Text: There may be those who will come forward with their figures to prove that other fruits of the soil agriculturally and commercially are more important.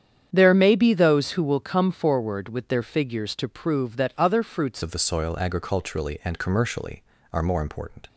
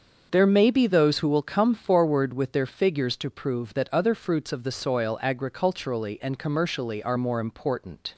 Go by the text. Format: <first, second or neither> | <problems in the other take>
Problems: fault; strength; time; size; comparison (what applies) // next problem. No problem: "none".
second | starts louder than the rest; strong; until 1.3 s; 8.5 dB; also in the second // changes voice at "of"; from 4.8 s on; 3.2 s long